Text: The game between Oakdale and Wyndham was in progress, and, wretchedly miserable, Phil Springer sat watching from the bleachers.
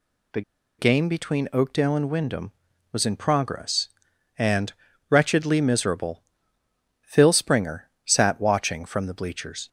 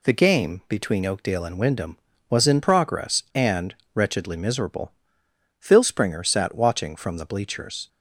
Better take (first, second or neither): second